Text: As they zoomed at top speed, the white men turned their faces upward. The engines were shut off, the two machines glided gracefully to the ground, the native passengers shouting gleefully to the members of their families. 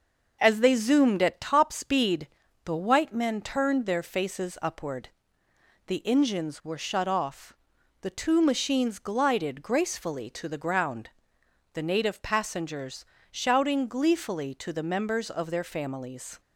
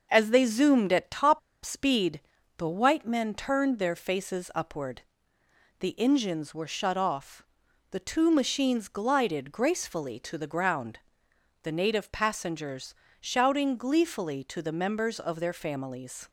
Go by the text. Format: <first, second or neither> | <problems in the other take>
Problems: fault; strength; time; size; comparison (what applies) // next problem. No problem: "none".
first | starts louder than the rest; noticeable; until 1.1 s; 6 dB; noticeable in the first // pauses between "top" and "speed"; slight; at 1.3 s; 0.25 s long // pauses between "passengers" and "shouting"; slight; at 12.9 s; 0.26 s long; slight in the first